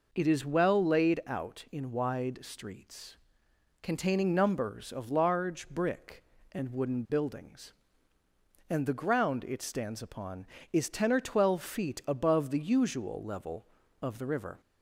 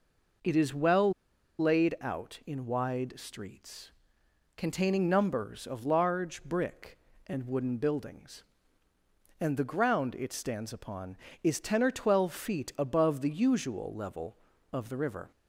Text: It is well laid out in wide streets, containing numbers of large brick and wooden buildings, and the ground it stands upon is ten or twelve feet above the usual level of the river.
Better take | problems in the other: first | pauses between "well" and "laid"; noticeable; at 1.1 s; 0.46 s long

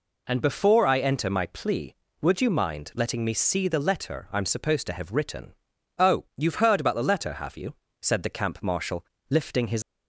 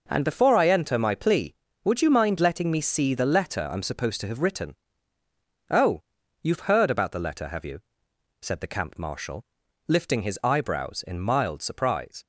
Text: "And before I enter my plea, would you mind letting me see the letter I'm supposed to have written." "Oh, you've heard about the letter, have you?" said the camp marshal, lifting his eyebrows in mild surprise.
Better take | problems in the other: second | stops before "eyebrows in mild surprise"; at 9.8 s

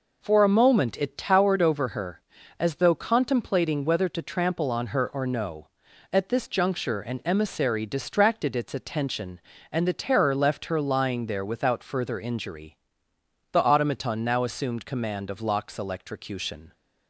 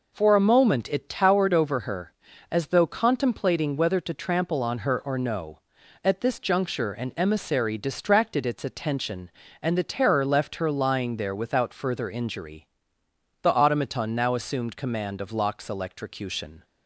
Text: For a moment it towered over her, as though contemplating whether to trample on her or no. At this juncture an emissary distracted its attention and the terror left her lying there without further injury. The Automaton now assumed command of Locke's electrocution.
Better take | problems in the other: neither | none

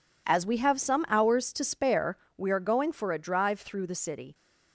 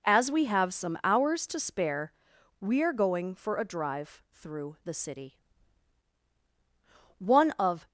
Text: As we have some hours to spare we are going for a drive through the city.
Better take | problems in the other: first | pauses between "spare" and "we"; noticeable; at 2.1 s; 0.48 s long; slight in the first // goes on to say "One of"; noticeable; from 7.1 s on; 0.68 s long

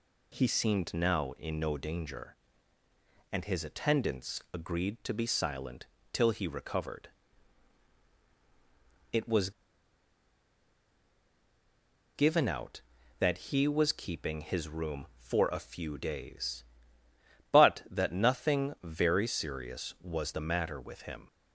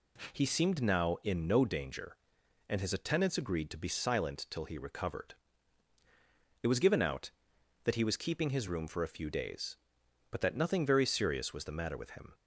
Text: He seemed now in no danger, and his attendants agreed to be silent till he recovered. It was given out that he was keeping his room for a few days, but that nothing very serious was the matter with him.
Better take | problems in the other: second | pauses between "silent" and "till"; slight; at 5.8 s; 0.26 s long // pauses between "was" and "given"; strong; at 9.5 s; 2.6 s long

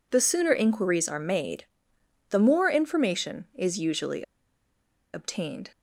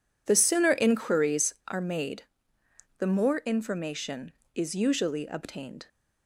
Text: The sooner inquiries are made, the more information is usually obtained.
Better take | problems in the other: second | pauses between "usually" and "obtained"; noticeable; at 4.2 s; 0.91 s long

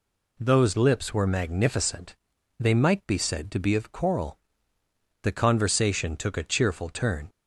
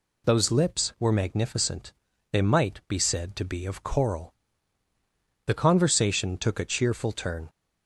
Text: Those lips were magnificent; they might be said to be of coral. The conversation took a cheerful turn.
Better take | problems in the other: neither | none

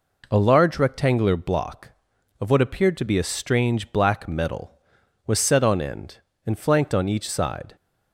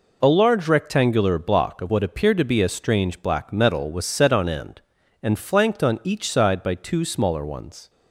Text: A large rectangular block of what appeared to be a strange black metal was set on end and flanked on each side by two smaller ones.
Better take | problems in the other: second | stops before "by two smaller ones"; at 7.7 s

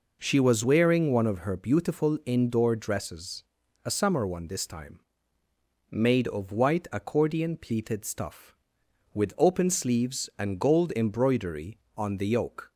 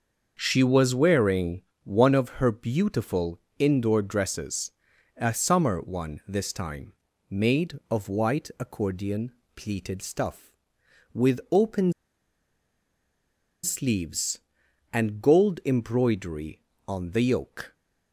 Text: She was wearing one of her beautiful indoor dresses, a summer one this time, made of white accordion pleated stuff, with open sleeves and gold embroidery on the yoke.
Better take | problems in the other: first | starts louder than the rest; until 1.3 s; 6.5 dB // pauses between "wearing" and "one"; slight; at 1.6 s; 0.20 s long // pauses between "beautiful" and "indoor"; slight; at 3.4 s; 0.18 s long // pauses between "accordion" and "pleated"; slight; at 9.3 s; 0.24 s long // pauses between "open" and "sleeves"; strong; at 11.9 s; 1.7 s long

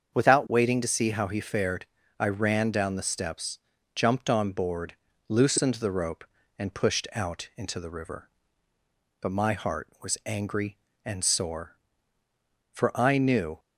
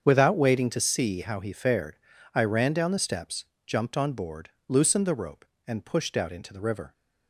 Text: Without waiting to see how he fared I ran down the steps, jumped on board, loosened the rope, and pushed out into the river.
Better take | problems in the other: second | starts louder than the rest; until 1.1 s; 7 dB; strong in the second // pauses between "fared" and "I"; slight; at 1.8 s; 0.32 s long; also in the second // goes on to say "But my heart was angry and sore for I knew"; strong; from 9.1 s on; 4.4 s long

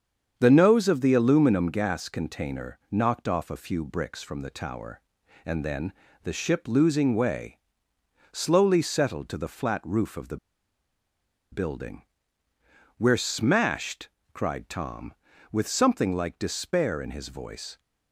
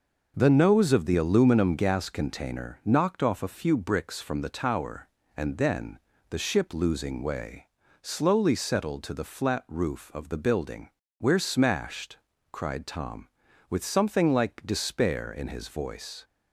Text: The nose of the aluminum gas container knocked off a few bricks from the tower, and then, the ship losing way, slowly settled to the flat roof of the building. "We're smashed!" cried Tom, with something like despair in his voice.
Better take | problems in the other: second | starts louder than the rest; strong; until 1.3 s; 7.5 dB; noticeable in the second // pauses between "the" and "building"; at 10.3 s; 1.1 s long

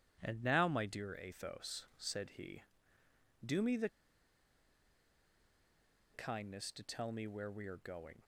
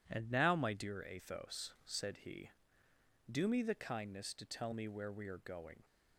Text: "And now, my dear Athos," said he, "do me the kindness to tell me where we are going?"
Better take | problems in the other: second | pauses between "the" and "kindness"; strong; at 3.8 s; 2.2 s long

